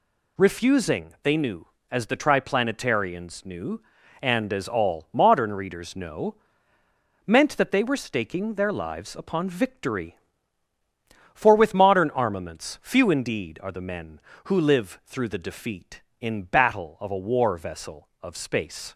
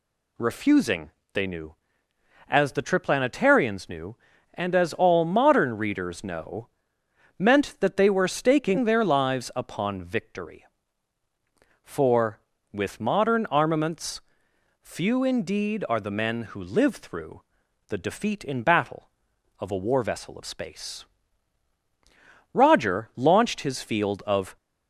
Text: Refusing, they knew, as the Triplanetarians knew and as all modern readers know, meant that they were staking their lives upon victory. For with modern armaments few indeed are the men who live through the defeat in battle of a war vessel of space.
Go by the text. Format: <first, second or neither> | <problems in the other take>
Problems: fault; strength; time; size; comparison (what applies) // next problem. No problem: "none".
first | pauses between "armaments" and "few"; noticeable; at 14.2 s; 0.62 s long // pauses between "through" and "the"; noticeable; at 17.4 s; 0.46 s long // goes on to say "Roger launched his field of"; strong; from 22.5 s on; 2.0 s long